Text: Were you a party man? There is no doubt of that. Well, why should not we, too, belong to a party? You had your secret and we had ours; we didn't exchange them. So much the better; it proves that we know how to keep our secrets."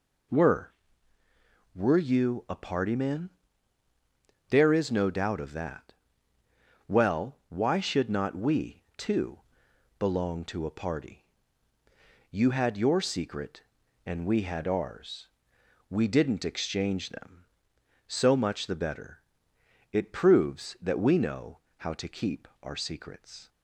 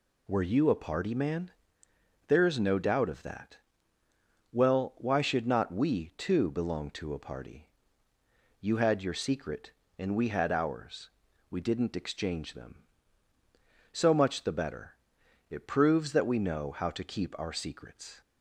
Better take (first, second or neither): second